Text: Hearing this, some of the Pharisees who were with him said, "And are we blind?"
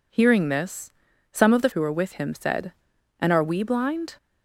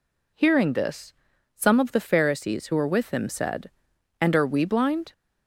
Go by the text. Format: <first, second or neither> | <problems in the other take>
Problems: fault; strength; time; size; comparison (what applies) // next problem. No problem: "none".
second | skips "Pharisees"; at 1.7 s